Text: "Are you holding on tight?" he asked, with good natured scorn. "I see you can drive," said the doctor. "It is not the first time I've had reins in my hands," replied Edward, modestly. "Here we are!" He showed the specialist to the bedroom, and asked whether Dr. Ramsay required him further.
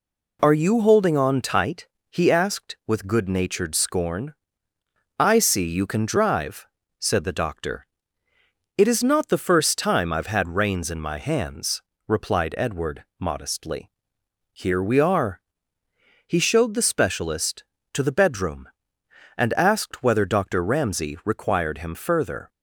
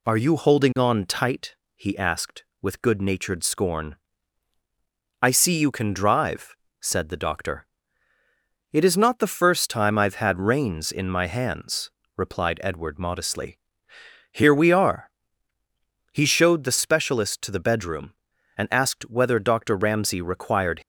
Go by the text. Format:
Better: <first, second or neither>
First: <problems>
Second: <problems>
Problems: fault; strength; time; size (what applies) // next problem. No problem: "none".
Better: first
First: none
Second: stops before "him further"; at 20.8 s